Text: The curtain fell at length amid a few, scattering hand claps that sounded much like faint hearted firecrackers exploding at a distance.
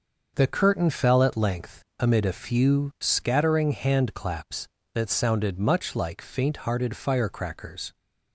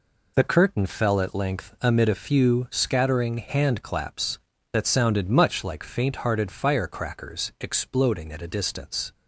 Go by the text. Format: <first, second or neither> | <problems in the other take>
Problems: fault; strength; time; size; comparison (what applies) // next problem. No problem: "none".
second | starts louder than the rest; until 1.3 s; 6.5 dB // pauses between "length" and "amid"; slight; at 1.8 s; 0.16 s long // stops before "exploding at a distance"; at 7.9 s